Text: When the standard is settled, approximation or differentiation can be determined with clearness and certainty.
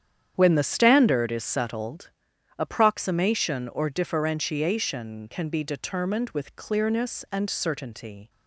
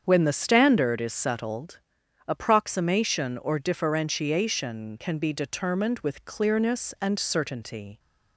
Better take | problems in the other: second | gets quieter; strong; throughout; 11.5 dB // starts louder than the rest; strong; until 1.3 s; 9 dB; strong in the second

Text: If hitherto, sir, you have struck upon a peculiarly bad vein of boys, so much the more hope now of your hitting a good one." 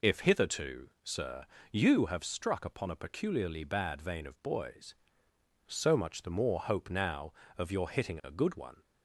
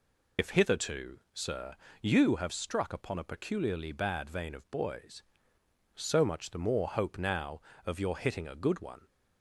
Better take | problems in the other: first | loses the start of "If"; at 0.3 s; 60 ms

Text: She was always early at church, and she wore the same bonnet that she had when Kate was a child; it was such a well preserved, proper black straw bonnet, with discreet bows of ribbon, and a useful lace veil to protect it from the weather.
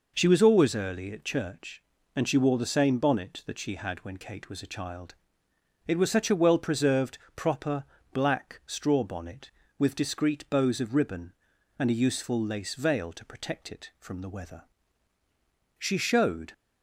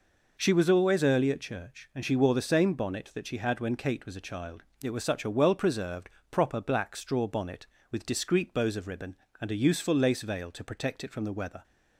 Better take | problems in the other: second | pauses between "proper" and "black"; slight; at 7.8 s; 0.30 s long // goes on to say "She showed"; noticeable; from 15.7 s on; 0.74 s long

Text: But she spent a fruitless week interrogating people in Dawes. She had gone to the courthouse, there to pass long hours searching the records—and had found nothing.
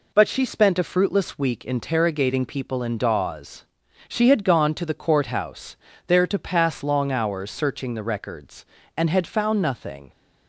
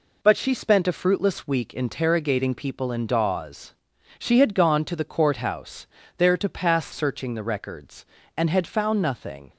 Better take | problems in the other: first | skips "long hours"; at 6.9 s

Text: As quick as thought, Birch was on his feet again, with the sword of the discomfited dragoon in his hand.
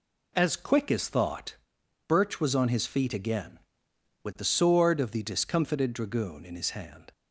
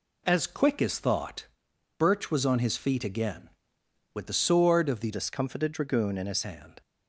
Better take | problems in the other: first | changes voice from "discomfited" to "his"; from 5.1 to 6.4 s; 1.3 s long

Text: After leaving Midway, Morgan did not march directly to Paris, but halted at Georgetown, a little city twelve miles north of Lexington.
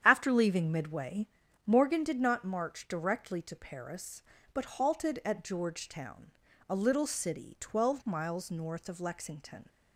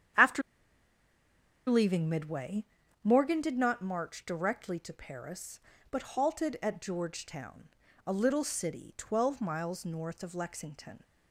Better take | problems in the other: first | starts louder than the rest; strong; until 2.4 s; 9 dB; strong in the first // pauses between "After" and "leaving"; strong; at 0.4 s; 1.2 s long

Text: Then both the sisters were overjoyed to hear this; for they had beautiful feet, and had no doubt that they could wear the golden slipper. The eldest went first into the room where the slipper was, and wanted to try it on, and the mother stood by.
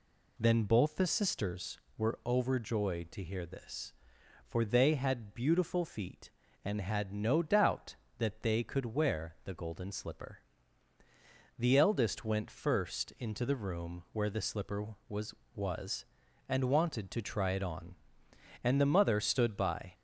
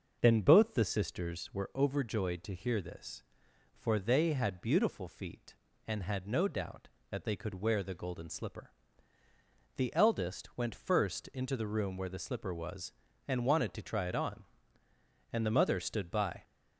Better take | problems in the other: second | says "was" twice; at 15.5 s

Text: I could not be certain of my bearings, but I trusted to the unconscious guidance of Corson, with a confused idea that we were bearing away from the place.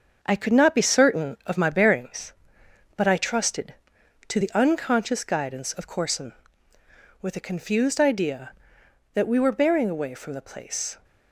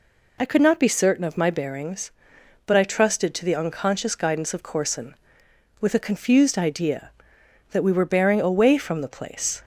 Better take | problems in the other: second | gets quieter; noticeable; throughout; 5.5 dB

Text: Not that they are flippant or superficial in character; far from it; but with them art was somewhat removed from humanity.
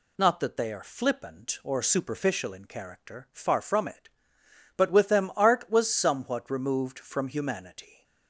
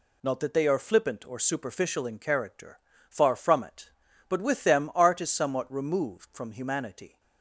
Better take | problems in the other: first | says "is" for "was"; at 5.2 s

